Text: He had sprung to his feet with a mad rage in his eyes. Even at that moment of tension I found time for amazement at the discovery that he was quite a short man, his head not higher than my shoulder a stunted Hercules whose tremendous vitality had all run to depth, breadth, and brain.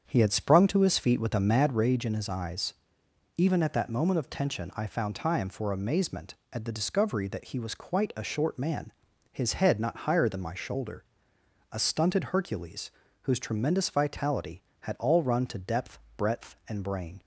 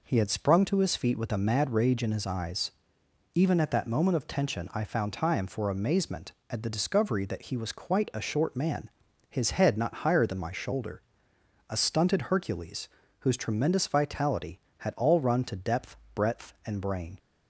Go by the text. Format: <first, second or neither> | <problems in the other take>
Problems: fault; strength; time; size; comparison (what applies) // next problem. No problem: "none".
second | starts louder than the rest; strong; until 1.9 s; 7.5 dB // pauses between "shoulder" and "a"; noticeable; at 11.0 s; 0.70 s long; noticeable in the second // pauses between "Hercules" and "whose"; slight; at 12.9 s; 0.30 s long; slight in the second